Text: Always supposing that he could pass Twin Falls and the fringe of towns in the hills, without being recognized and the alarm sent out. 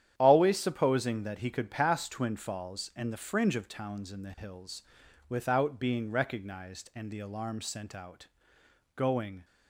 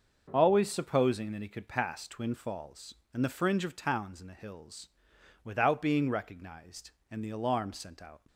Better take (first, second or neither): second